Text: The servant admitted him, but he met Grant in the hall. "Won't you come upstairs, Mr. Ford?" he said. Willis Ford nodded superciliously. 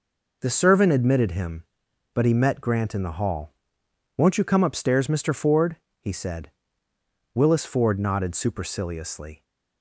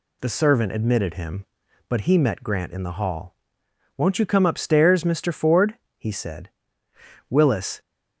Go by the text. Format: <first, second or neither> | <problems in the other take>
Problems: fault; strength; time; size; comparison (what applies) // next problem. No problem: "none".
first | stops before "Ford nodded superciliously"; at 7.7 s